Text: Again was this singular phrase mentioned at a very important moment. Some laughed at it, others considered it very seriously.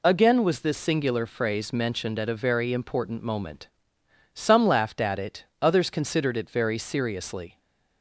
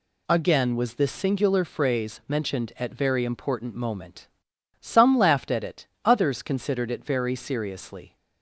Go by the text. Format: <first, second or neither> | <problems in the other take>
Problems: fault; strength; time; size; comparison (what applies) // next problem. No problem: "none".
first | skips "a"; at 2.9 s